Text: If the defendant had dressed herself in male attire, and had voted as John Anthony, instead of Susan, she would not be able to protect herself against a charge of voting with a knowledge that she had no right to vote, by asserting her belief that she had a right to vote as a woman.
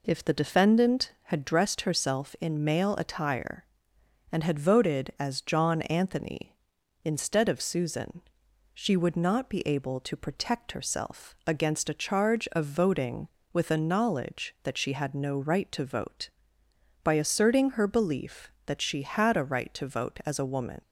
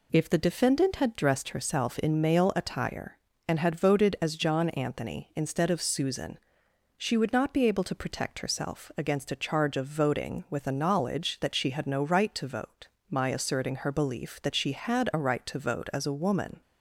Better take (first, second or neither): first